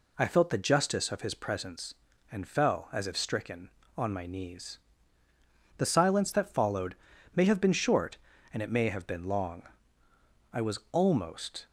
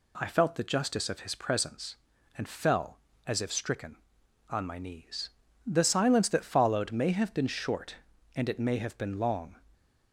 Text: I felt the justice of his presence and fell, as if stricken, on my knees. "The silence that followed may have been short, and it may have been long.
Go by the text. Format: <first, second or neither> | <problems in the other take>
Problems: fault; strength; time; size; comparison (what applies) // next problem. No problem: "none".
second | pauses between "followed" and "may"; at 6.9 s; 0.40 s long // goes on to say "I was almost"; noticeable; from 10.5 s on; 1.1 s long